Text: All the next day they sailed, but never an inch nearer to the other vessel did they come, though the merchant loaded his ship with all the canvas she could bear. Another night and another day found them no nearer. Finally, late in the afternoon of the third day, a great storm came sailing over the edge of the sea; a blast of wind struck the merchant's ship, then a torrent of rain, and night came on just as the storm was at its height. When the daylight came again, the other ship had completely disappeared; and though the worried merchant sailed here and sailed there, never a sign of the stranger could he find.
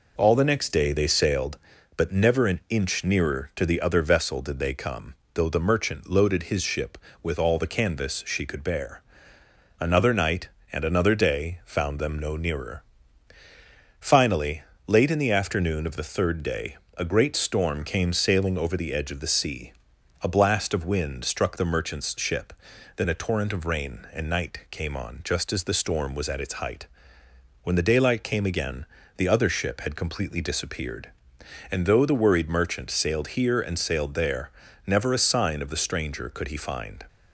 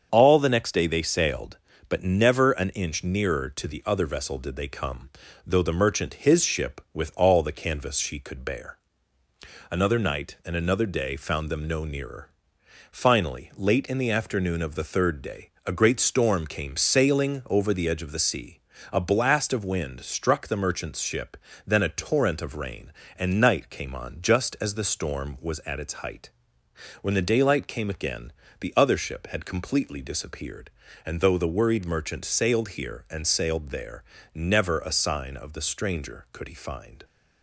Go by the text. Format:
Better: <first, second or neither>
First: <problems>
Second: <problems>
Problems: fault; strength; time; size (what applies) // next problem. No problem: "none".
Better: first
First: none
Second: starts louder than the rest; until 1.1 s; 7 dB // skips "loaded"; at 6.1 s